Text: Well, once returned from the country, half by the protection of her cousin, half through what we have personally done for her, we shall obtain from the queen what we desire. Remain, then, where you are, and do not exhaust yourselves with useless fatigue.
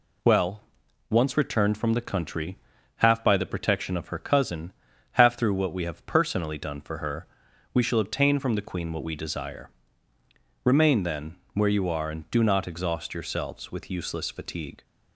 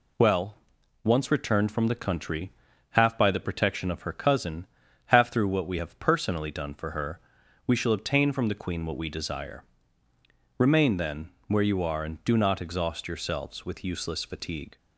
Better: neither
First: none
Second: none

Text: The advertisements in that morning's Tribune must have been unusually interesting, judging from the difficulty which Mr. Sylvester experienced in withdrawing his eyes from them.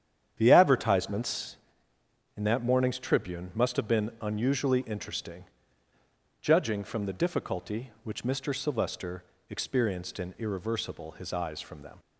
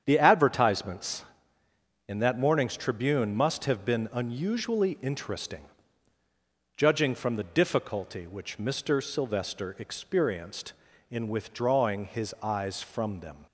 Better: second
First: starts louder than the rest; strong; until 1.3 s; 9 dB // pauses between "Sylvester" and "experienced"; slight; at 9.2 s; 0.26 s long // says "irreversible" for "withdrawing"; at 10.3 s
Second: starts louder than the rest; strong; until 1.0 s; 8.5 dB

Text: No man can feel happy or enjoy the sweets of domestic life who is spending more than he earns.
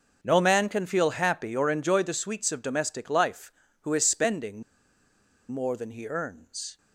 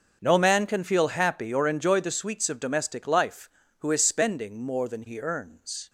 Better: second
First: starts louder than the rest; until 1.2 s; 6.5 dB // pauses between "spending" and "more"; noticeable; at 4.6 s; 0.88 s long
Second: starts louder than the rest; until 1.2 s; 6.5 dB

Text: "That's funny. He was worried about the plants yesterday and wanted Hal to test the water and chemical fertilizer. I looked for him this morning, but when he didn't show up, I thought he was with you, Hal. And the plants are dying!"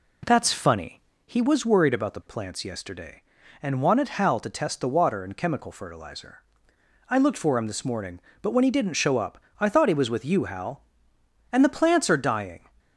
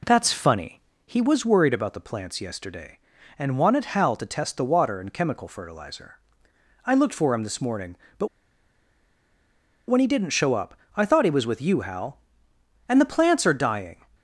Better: first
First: none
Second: pauses between "but" and "when"; strong; at 8.2 s; 1.6 s long

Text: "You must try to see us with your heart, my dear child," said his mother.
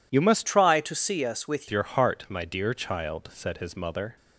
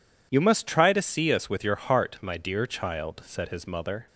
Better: second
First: changes voice from "try" to "with"; from 0.4 to 1.6 s; 1.2 s long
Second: none

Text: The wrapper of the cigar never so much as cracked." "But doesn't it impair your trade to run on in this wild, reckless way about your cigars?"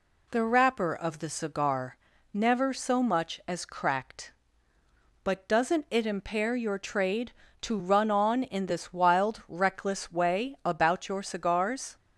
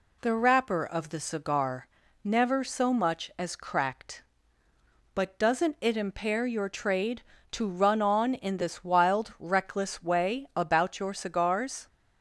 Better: neither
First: pauses between "cigar" and "never"; at 1.9 s; 0.38 s long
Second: pauses between "cigar" and "never"; at 1.8 s; 0.38 s long

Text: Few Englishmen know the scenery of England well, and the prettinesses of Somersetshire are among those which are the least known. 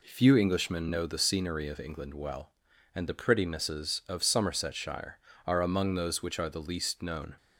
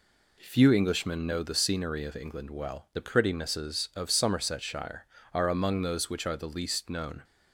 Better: first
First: none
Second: skips "and"; at 2.9 s

